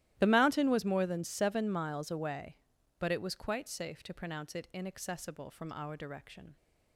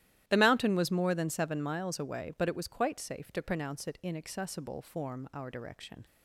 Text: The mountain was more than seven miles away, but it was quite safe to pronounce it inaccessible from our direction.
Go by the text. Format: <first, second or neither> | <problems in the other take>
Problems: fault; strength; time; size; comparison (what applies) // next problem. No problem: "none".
first | starts louder than the rest; strong; until 1.2 s; 13 dB; strong in the first // says "form" for "from"; at 4.8 s